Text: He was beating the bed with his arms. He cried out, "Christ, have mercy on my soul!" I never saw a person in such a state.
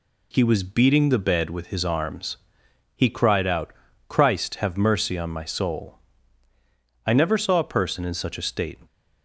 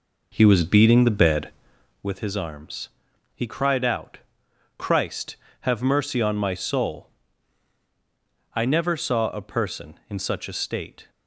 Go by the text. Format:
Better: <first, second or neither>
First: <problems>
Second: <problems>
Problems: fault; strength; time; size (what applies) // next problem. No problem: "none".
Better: first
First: none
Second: starts louder than the rest; noticeable; until 2.1 s; 5 dB